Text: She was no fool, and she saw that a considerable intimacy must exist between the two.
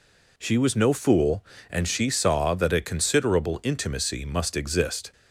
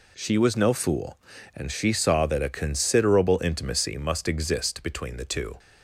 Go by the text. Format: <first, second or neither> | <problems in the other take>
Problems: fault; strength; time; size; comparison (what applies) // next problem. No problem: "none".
second | stops before "between the two"; at 5.1 s